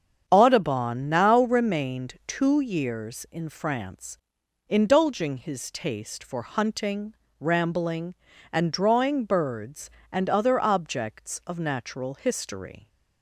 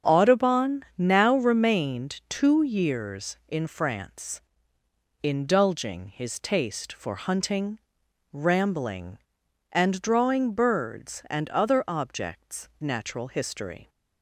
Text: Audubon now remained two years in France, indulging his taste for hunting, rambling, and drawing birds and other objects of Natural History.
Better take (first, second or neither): first